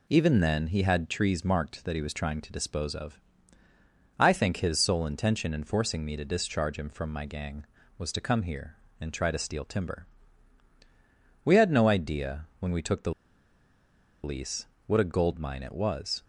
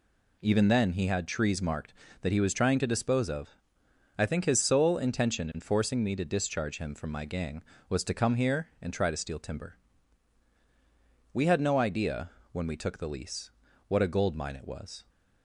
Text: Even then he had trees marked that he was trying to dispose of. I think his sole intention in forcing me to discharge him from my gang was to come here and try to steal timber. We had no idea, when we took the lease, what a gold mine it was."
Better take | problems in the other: second | pauses between "the" and "lease"; at 13.1 s; 1.1 s long

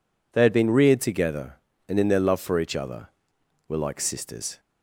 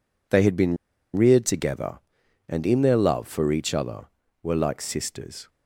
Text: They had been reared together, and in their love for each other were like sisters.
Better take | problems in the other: first | pauses between "been" and "reared"; at 0.7 s; 0.38 s long

